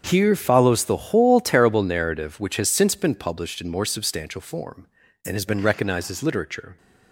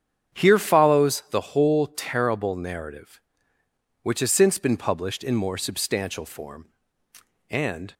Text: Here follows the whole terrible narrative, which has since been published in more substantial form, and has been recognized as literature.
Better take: first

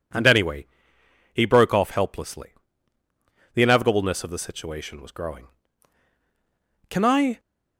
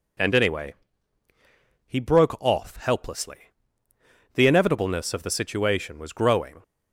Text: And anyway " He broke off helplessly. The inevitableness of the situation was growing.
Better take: second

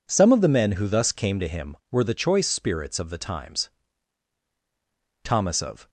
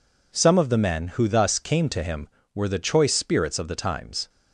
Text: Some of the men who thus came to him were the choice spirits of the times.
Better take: second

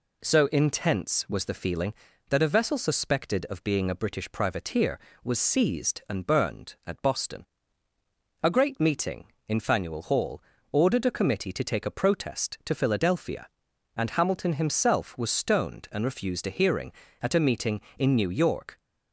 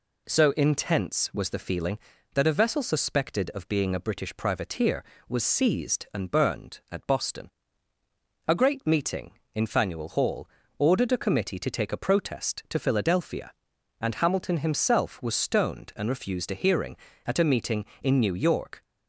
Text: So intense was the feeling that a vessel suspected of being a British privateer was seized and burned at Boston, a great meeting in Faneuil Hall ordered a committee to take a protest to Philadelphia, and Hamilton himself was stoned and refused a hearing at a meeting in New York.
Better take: neither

